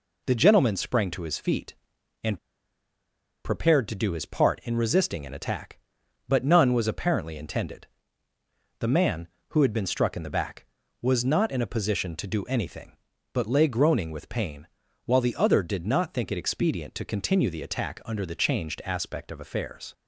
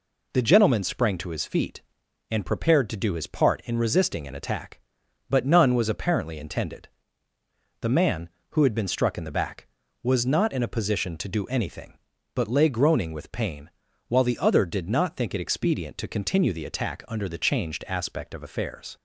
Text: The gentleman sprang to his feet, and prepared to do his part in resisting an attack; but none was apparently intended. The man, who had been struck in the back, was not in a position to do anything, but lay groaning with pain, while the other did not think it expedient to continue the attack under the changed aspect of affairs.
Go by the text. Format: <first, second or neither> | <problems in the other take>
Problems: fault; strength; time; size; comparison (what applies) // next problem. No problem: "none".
second | pauses between "and" and "prepared"; at 2.3 s; 1.0 s long